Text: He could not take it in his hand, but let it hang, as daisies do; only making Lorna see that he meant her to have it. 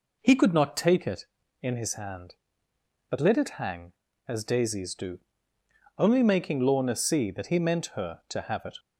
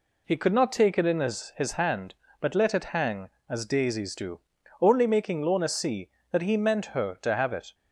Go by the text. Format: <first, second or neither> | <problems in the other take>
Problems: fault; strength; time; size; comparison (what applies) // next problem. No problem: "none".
first | says "his" twice; at 1.5 s